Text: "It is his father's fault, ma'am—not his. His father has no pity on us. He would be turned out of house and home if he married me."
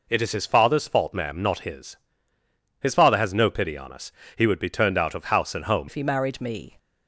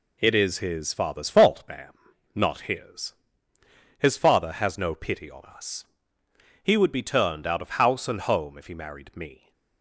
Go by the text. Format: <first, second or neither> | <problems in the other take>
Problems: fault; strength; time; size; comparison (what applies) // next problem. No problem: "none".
second | changes voice at "if"; from 5.8 s on; 0.9 s long